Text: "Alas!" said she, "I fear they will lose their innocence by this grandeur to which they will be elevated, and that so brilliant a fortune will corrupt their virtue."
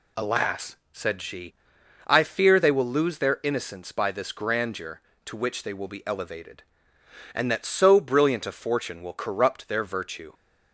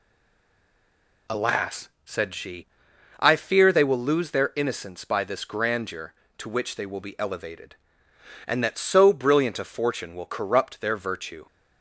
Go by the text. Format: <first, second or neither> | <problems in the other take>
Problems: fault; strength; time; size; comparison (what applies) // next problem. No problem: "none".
first | stays silent before the first word; noticeable; until 1.2 s; 1.2 s long